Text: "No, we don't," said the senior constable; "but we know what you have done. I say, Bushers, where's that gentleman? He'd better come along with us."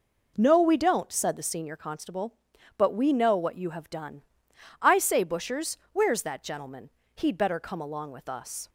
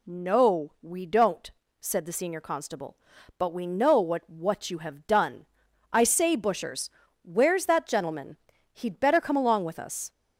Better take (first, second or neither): first